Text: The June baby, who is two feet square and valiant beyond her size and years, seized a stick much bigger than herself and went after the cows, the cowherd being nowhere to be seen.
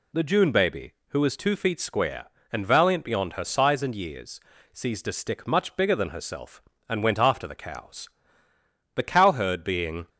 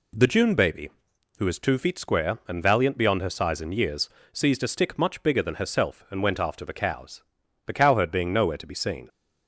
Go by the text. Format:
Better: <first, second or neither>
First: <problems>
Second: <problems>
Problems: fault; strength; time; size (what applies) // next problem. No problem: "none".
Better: second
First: stops before "nowhere to be seen"; at 10.0 s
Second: none